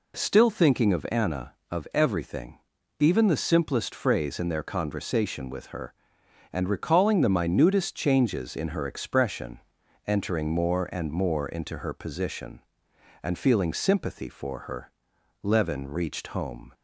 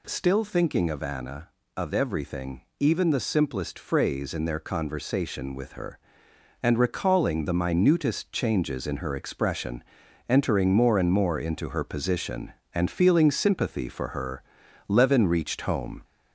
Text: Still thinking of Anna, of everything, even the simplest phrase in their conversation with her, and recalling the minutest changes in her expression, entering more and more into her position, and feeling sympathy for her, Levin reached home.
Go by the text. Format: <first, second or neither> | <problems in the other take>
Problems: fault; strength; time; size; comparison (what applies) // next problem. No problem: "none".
first | gets louder; slight; throughout; 2 dB